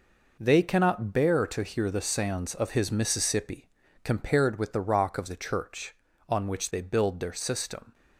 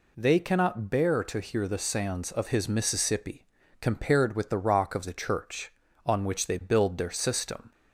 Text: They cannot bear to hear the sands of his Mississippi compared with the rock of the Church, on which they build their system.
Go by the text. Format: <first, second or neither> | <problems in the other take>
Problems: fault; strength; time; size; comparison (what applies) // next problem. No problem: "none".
second | gets quieter; strong; throughout; 9.5 dB // pauses between "Mississippi" and "compared"; slight; at 3.6 s; 0.34 s long; slight in the second